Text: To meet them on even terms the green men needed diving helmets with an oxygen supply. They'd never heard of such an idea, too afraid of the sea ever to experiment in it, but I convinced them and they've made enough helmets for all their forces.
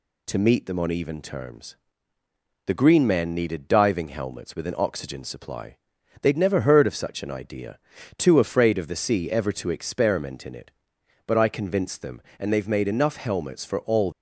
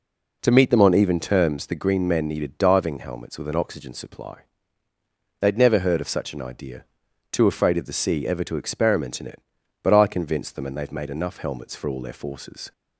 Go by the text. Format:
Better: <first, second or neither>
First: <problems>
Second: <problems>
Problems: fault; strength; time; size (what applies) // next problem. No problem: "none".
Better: second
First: pauses between "terms" and "the"; noticeable; at 1.7 s; 0.90 s long // stops before "their forces"; at 14.1 s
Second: none